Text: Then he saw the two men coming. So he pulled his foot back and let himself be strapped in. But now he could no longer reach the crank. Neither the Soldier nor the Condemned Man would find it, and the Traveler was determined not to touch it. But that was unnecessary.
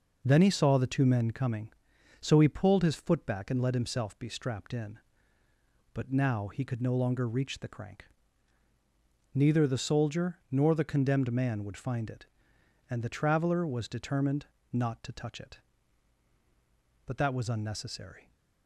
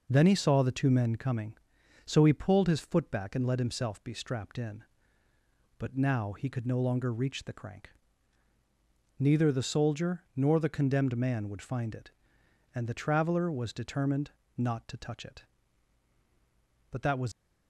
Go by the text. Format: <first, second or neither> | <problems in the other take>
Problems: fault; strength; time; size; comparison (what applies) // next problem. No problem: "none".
first | pauses between "determined" and "not"; slight; at 14.3 s; 0.26 s long; slight in the first // stops before "unnecessary"; at 17.3 s